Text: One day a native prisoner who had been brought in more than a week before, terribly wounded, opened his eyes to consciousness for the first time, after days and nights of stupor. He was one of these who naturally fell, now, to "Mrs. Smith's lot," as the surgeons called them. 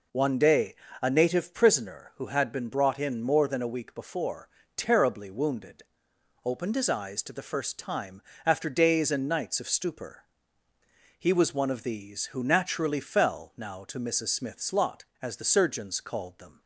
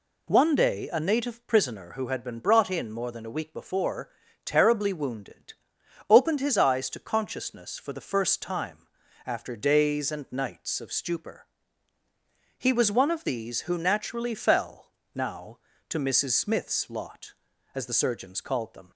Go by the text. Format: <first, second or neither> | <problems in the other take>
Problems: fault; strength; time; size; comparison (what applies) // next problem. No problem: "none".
second | pauses between "day" and "a"; slight; at 0.7 s; 0.28 s long // skips "consciousness for"; at 7.3 s